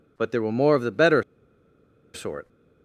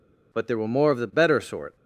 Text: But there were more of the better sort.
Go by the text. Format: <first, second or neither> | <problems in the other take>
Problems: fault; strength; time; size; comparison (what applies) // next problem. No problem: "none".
second | pauses between "better" and "sort"; noticeable; at 1.2 s; 0.92 s long